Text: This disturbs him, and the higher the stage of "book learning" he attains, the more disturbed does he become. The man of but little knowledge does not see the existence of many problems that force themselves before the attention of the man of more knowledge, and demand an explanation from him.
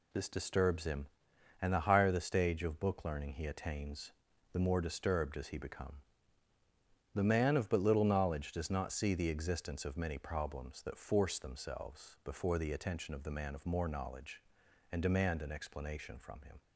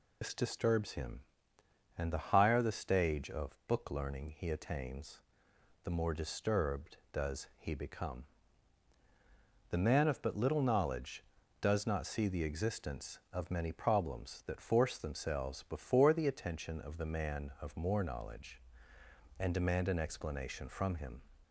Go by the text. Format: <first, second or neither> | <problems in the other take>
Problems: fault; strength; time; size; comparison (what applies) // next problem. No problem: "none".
first | loses the start of "This"; at 0.2 s; 90 ms